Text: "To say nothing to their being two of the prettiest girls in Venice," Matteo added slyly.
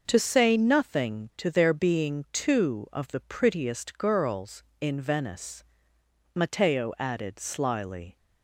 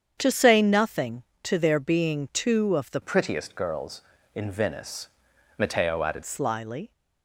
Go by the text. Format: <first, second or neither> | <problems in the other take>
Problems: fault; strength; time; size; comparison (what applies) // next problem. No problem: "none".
first | starts louder than the rest; strong; until 1.2 s; 8 dB // changes voice from "prettiest" to "added"; from 3.0 to 6.2 s; 3.2 s long